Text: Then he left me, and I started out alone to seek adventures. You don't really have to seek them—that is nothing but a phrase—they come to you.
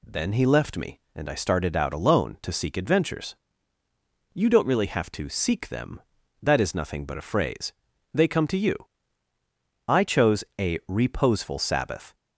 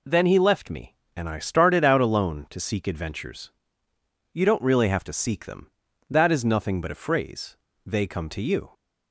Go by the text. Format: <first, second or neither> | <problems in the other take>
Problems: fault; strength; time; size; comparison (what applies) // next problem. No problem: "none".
second | goes on to say "I chose a reposeful Sabbath"; strong; from 9.8 s on; 2.2 s long